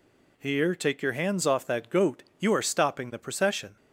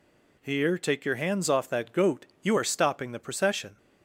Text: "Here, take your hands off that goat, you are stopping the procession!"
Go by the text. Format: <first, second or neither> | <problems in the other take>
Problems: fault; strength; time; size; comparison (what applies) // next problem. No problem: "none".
neither | none